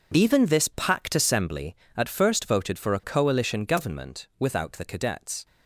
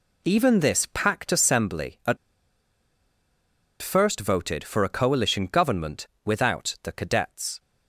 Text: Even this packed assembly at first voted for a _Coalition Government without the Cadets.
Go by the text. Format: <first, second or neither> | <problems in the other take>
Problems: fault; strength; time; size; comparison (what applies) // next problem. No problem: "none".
first | pauses between "at" and "first"; strong; at 2.1 s; 1.6 s long // pauses between "Government" and "without"; slight; at 6.0 s; 0.16 s long